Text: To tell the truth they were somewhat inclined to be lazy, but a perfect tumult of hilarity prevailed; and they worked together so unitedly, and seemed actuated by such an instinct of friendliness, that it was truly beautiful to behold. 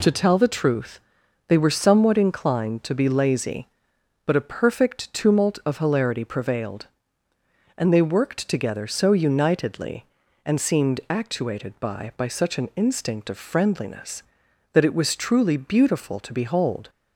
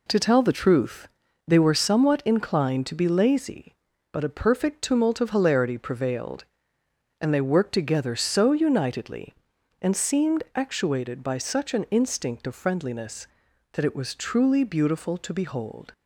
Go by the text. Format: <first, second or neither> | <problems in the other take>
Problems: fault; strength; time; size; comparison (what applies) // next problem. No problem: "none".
second | pauses between "truth" and "they"; noticeable; at 0.9 s; 0.48 s long; also in the second // says "by" twice; at 12.1 s